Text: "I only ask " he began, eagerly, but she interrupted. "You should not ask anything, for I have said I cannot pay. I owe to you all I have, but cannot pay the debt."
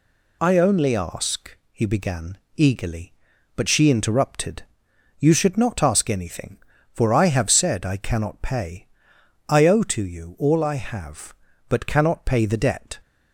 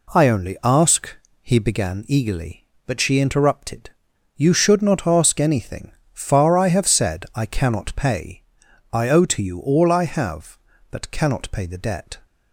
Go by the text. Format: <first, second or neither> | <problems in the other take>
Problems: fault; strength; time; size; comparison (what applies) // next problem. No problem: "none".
first | says "far" for "for"; at 6.1 s